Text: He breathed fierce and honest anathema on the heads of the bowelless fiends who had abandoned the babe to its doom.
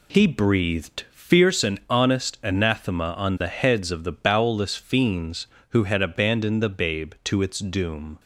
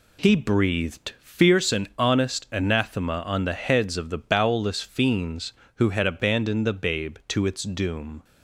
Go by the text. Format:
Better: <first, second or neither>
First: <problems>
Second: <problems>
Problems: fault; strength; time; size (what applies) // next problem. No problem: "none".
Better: neither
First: none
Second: none